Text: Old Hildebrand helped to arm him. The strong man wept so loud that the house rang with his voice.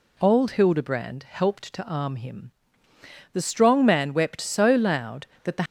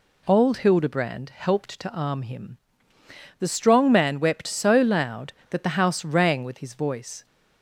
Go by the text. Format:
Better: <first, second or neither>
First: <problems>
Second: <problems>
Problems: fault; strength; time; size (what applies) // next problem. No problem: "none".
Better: second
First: stops before "house rang with his voice"; at 5.6 s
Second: none